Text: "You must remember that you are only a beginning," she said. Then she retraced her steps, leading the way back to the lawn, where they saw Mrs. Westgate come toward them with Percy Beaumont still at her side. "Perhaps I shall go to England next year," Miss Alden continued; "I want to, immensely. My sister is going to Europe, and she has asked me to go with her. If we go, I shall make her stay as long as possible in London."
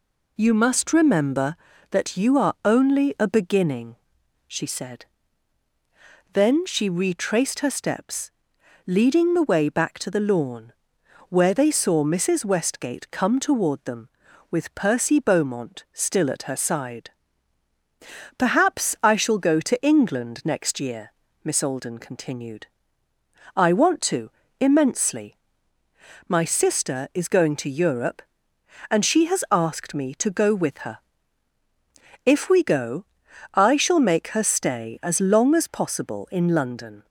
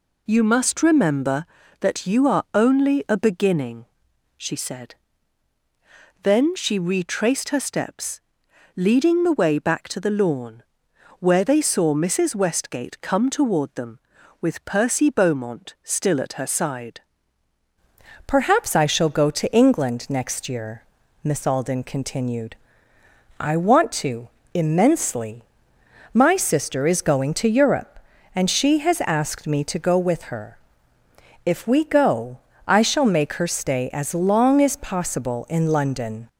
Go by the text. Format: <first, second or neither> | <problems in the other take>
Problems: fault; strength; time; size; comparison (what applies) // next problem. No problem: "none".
first | changes voice at "Perhaps"; from 18.2 s on; 18.0 s long